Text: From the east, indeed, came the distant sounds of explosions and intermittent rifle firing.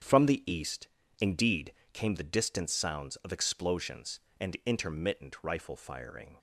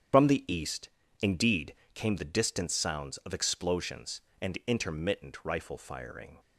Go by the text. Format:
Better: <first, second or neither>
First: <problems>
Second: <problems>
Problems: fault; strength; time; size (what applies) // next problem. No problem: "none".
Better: first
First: starts louder than the rest; strong; until 1.4 s; 8 dB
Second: loses the start of "From"; at 0.1 s; 105 ms // starts louder than the rest; strong; until 1.5 s; 9 dB